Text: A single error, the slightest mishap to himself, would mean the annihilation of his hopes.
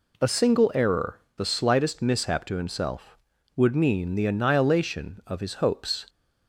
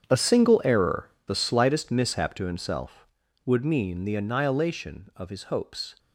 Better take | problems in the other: first | gets quieter; strong; throughout; 15.5 dB

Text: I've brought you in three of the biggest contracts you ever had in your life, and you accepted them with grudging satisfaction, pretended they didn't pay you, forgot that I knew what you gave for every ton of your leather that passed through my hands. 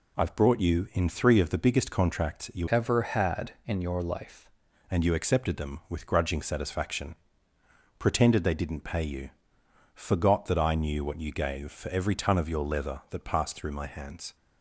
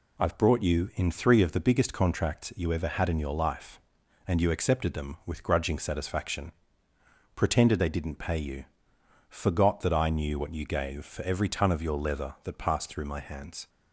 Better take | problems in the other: second | changes voice from "ever" to "life"; from 2.6 to 4.5 s; 1.9 s long

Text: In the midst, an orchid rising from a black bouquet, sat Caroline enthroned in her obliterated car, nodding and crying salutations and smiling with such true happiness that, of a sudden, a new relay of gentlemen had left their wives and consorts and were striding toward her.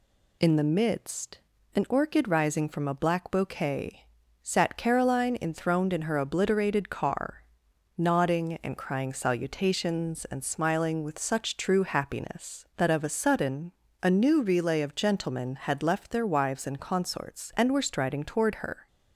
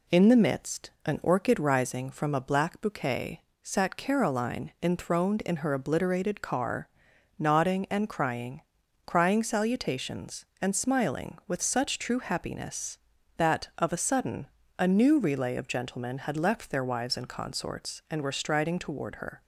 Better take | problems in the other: first | says "crying" twice; at 9.0 s

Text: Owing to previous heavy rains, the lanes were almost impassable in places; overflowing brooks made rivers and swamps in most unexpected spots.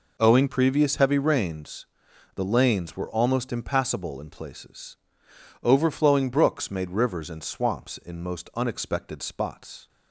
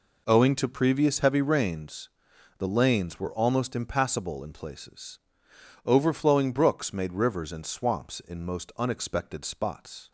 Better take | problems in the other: second | skips "to"; at 0.4 s

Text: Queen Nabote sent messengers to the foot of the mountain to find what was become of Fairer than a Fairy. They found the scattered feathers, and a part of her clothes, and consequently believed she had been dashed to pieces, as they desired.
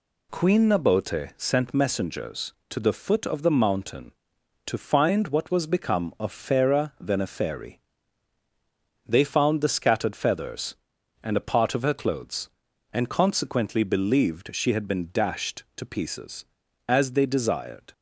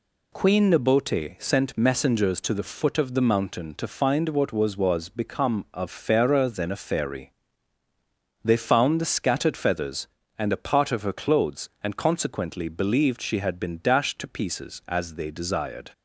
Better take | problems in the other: first | says "was" twice; at 4.7 s

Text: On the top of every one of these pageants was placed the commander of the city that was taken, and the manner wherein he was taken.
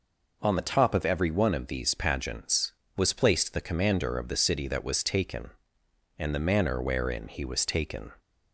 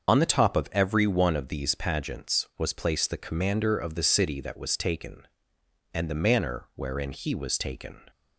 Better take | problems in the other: first | loses the start of "On"; at 0.0 s; 50 ms // starts louder than the rest; until 1.1 s; 6.5 dB

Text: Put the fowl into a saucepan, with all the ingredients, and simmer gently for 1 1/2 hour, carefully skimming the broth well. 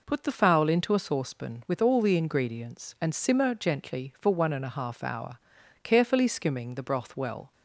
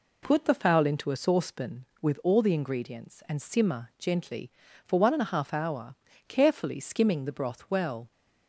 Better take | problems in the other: neither | none

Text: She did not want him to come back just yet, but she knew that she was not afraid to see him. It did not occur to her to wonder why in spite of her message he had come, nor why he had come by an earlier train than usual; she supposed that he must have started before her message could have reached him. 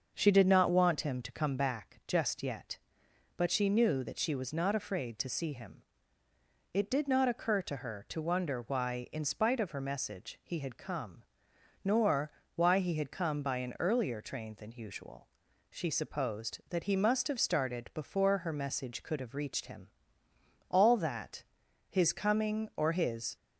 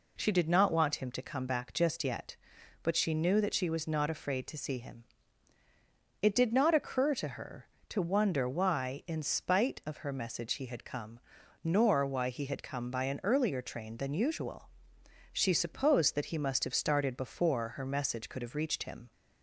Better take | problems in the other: second | starts louder than the rest; until 1.1 s; 6.5 dB // pauses between "nor" and "why"; slight; at 12.3 s; 0.24 s long // goes on to say "All that his coming or his"; strong; from 20.7 s on; 2.6 s long

